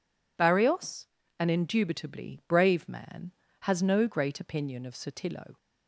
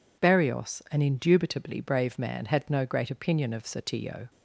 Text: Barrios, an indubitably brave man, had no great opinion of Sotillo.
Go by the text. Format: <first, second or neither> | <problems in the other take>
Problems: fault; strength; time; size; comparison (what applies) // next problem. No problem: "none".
second | says "has" for "had"; at 3.6 s